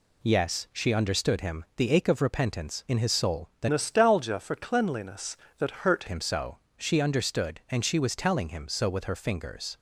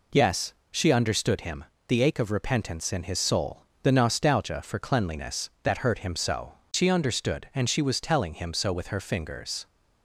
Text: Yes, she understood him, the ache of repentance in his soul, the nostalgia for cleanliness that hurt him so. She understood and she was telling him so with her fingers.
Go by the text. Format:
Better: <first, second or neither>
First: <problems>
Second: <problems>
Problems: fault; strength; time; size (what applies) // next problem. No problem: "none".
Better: second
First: changes voice from "nostalgia" to "hurt"; from 3.6 to 6.0 s; 2.4 s long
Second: none